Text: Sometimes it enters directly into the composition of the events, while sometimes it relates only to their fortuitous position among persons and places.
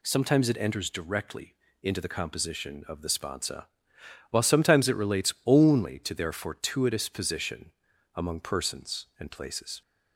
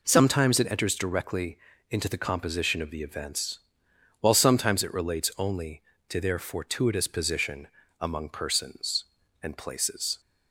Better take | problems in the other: second | pauses between "directly" and "into"; slight; at 1.5 s; 0.30 s long; slight in the second // says "sponsa" for "events"; at 3.0 s // pauses between "position" and "among"; at 7.7 s; 0.44 s long; slight in the second

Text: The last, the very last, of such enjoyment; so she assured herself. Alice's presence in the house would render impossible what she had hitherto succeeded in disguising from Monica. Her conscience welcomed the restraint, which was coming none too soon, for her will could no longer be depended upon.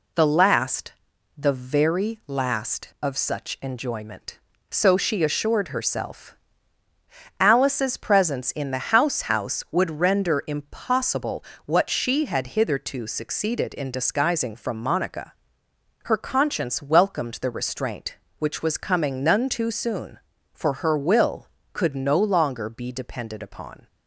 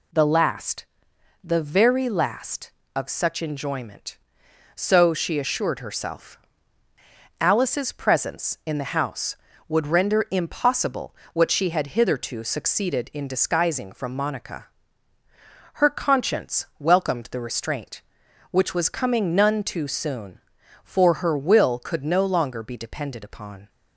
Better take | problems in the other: second | says "house" twice; at 9.3 s // pauses between "impossible" and "what"; slight; at 11.4 s; 0.20 s long; slight in the second

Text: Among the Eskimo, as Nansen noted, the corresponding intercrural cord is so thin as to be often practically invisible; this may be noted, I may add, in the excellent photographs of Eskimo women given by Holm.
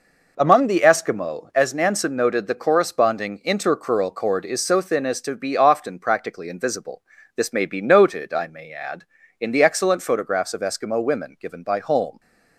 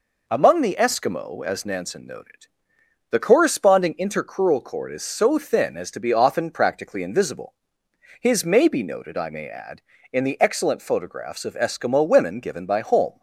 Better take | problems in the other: first | says "his" for "this"; at 8.2 s

